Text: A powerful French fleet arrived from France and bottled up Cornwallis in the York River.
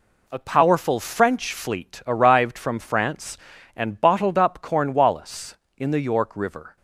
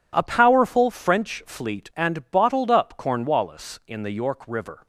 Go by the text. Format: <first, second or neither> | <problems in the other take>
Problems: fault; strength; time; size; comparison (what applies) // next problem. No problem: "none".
first | skips "arrived from France"; at 1.9 s